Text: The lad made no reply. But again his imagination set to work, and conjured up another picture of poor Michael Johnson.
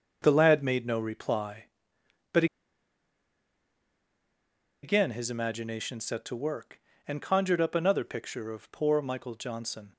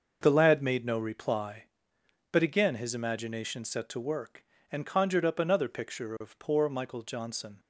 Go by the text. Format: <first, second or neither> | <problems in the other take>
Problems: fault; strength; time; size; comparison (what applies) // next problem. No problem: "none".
second | starts louder than the rest; until 1.2 s; 6 dB; also in the second // pauses between "But" and "again"; strong; at 2.4 s; 2.3 s long